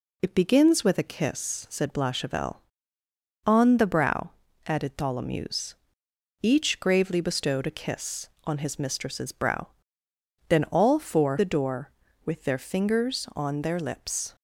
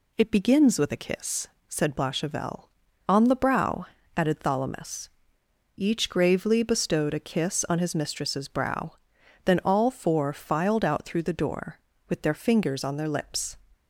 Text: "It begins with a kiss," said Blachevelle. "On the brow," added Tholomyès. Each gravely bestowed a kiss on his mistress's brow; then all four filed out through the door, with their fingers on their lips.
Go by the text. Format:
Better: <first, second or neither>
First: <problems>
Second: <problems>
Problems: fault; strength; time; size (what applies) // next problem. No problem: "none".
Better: second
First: skips "filed out through"; at 11.3 s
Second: none